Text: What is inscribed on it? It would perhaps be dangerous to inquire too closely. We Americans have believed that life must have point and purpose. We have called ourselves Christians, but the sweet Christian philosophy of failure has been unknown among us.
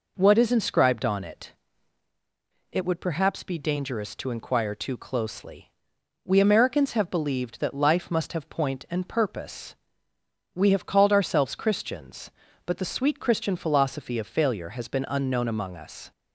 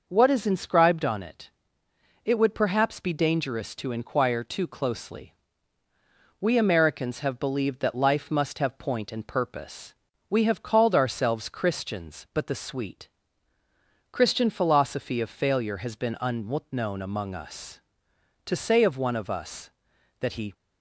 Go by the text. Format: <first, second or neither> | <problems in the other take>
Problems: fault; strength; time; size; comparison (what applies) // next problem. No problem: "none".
first | pauses between "sweet" and "Christian"; at 13.0 s; 1.0 s long // goes on to say "To say of one of us that he"; strong; from 18.4 s on; 2.0 s long